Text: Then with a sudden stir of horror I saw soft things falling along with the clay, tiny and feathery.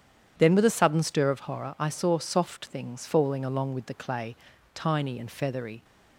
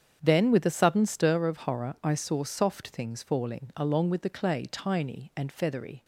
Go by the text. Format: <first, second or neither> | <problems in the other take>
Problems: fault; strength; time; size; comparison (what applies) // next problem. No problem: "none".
neither | starts louder than the rest; strong; the same in both